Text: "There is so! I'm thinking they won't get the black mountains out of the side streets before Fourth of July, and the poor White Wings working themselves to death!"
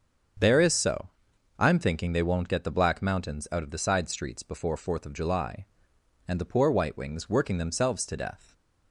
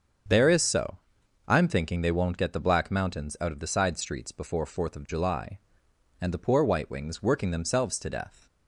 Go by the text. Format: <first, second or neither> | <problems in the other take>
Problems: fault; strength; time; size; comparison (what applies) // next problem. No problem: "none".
neither | starts louder than the rest; the same in both